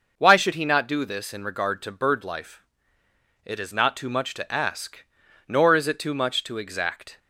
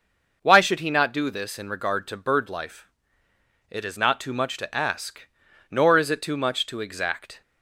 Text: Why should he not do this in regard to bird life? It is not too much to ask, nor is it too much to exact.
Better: neither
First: none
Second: none

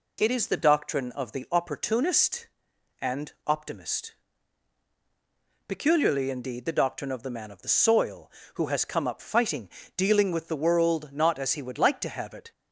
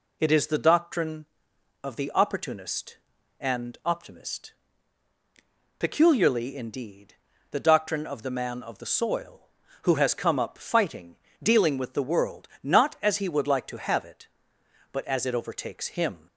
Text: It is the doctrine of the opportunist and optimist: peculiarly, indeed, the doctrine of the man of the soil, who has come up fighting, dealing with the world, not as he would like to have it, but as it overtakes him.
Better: second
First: pauses between "and" and "optimist"; slight; at 3.3 s; 0.16 s long // stops before "but as it overtakes him"; at 12.5 s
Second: none

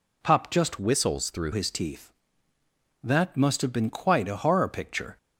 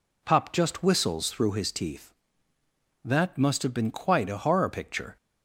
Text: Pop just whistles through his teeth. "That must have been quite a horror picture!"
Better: second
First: changes voice from "whistles" to "through"; from 0.7 to 1.5 s; 0.8 s long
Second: none

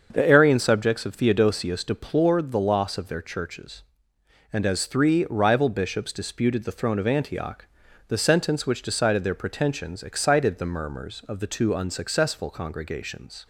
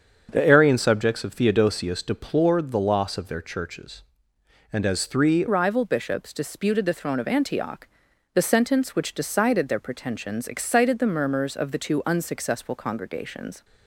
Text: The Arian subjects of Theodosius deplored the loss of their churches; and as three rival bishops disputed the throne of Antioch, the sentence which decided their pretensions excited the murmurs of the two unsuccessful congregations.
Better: first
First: starts louder than the rest; until 1.1 s; 6.5 dB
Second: starts louder than the rest; until 1.3 s; 6.5 dB // changes voice at "rival"; from 5.4 s on; 8.2 s long

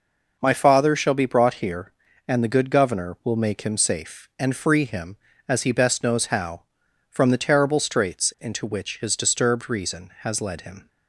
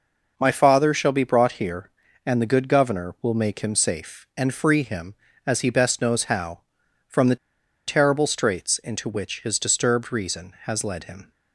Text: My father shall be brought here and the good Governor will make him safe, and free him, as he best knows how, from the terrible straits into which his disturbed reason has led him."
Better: first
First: none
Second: pauses between "the" and "terrible"; noticeable; at 7.3 s; 0.51 s long

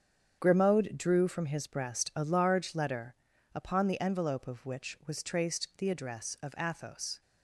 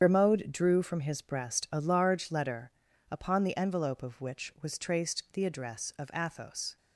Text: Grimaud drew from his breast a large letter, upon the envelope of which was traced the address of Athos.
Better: first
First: starts louder than the rest; strong; until 1.4 s; 8 dB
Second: loses the start of "Grimaud"; at 0.0 s; 60 ms // starts louder than the rest; strong; until 1.0 s; 8 dB

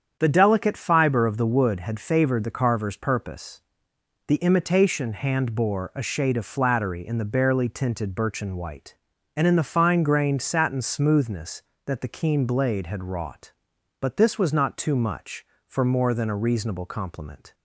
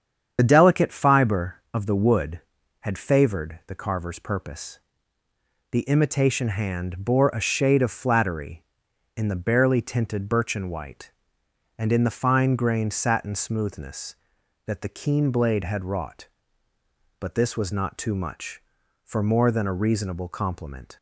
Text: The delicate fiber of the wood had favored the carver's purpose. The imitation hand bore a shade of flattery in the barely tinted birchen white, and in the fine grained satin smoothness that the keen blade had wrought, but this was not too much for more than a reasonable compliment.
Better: first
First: starts louder than the rest; strong; until 1.2 s; 8 dB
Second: loses the start of "The"; at 0.3 s; 40 ms // starts louder than the rest; strong; until 1.3 s; 8 dB

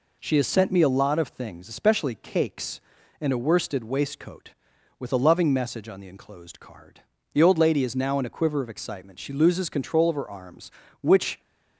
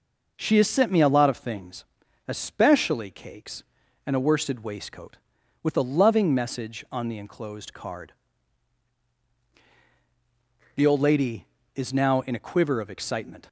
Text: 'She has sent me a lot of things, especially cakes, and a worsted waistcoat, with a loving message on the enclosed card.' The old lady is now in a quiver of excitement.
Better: second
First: goes on to say "She loses control of her arms which"; strong; from 9.2 s on; 2.2 s long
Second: none

